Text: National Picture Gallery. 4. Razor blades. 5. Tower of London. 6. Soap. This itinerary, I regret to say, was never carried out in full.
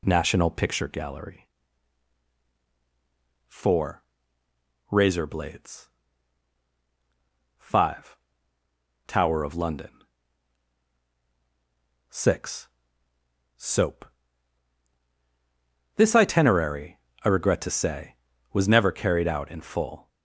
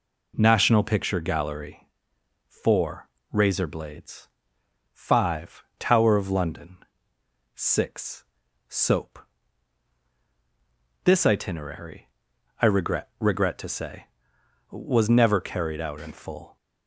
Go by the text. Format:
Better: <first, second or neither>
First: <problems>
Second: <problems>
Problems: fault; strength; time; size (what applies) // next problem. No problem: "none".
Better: first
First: none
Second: says "regret" twice; at 13.1 s